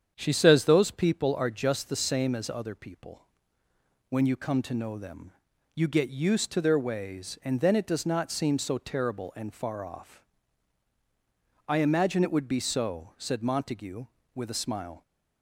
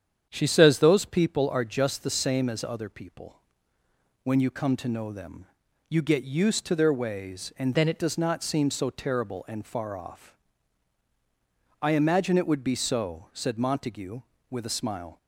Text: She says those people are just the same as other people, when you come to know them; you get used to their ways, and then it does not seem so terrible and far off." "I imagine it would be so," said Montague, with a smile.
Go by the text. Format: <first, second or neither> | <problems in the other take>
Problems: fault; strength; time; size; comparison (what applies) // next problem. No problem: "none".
first | starts louder than the rest; strong; until 1.3 s; 8.5 dB; strong in the first // changes voice from "then" to "it"; from 7.7 to 7.9 s; 0.2 s long